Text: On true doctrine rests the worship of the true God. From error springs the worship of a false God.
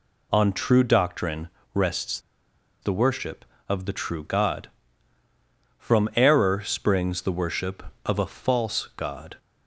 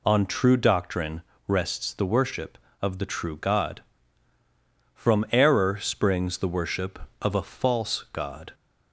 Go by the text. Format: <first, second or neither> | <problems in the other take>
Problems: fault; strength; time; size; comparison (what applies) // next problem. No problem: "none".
second | pauses between "doctrine" and "rests"; slight; at 1.4 s; 0.26 s long; slight in the second // pauses between "rests" and "the"; noticeable; at 2.1 s; 0.62 s long